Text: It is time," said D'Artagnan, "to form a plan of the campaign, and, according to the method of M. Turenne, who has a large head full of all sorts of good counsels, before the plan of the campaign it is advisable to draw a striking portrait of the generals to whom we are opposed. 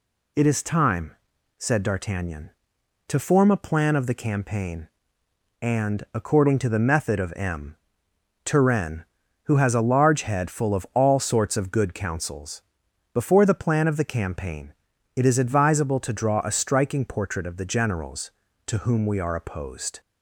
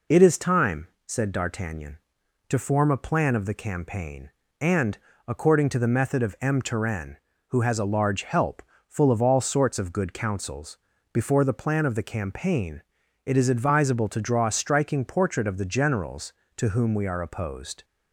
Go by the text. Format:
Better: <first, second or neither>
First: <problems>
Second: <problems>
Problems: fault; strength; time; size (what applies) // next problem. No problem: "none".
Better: first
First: pauses between "campaign" and "it"; at 14.7 s; 0.42 s long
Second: says "help" for "head"; at 8.2 s // pauses between "campaign" and "it"; at 12.8 s; 0.42 s long